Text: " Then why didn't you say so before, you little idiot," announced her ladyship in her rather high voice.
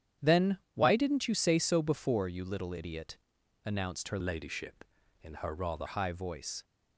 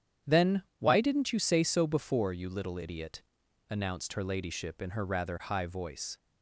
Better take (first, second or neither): second